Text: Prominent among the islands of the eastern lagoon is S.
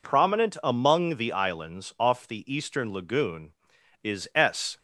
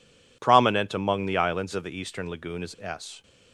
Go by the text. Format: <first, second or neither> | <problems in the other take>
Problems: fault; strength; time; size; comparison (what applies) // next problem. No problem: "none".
second | says "off" for "of"; at 1.9 s